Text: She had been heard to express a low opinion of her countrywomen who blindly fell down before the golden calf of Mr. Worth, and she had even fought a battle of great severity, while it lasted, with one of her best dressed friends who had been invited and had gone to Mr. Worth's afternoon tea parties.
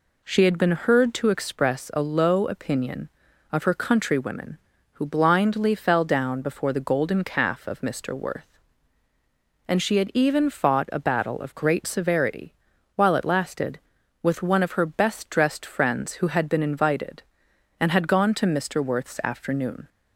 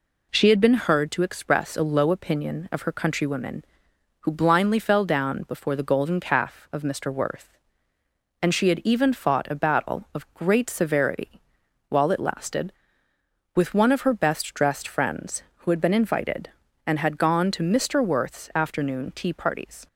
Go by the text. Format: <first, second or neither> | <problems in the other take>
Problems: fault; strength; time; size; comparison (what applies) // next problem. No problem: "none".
second | stops before "tea parties"; at 19.8 s